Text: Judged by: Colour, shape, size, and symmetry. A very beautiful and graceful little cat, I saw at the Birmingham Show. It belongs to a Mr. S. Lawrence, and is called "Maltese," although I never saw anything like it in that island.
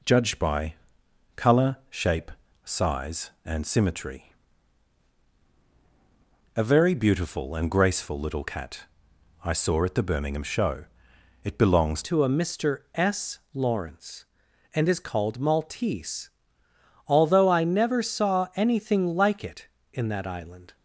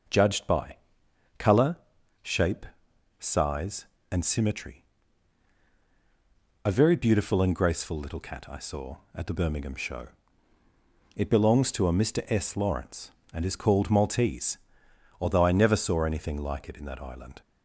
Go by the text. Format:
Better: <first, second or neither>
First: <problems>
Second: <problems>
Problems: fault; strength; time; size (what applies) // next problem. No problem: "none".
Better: second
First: changes voice at "to"; from 12.0 s on; 8.7 s long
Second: none